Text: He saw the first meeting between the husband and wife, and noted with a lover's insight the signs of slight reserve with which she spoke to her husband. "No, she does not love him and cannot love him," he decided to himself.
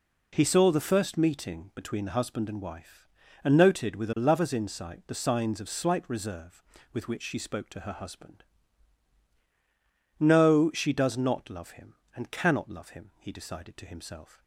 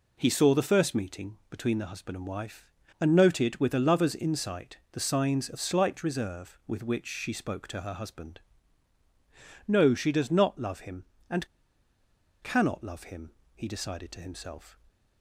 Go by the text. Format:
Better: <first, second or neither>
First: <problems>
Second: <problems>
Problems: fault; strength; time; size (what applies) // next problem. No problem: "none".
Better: first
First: none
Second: pauses between "and" and "cannot"; noticeable; at 11.4 s; 0.95 s long